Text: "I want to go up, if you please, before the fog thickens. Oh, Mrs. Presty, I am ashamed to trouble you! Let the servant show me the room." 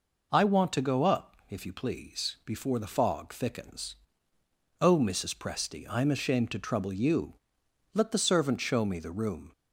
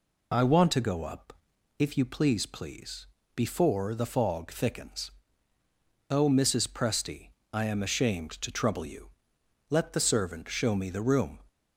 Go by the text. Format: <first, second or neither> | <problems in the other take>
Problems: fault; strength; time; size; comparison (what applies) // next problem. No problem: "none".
first | says "please" twice; at 2.4 s